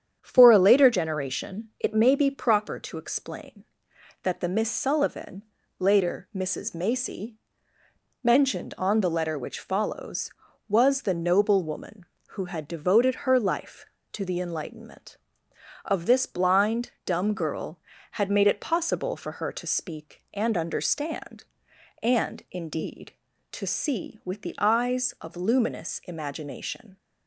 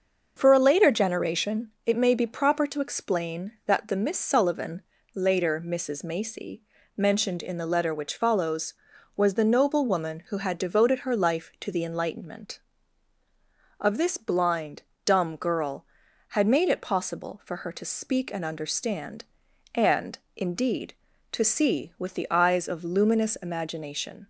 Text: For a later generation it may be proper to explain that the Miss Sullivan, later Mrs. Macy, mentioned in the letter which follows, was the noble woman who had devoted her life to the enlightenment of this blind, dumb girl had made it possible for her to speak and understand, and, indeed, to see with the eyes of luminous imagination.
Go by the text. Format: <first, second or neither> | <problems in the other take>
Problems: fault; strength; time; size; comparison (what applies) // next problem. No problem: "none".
second | starts louder than the rest; strong; until 1.2 s; 8.5 dB; noticeable in the second // says "on" for "in"; at 8.7 s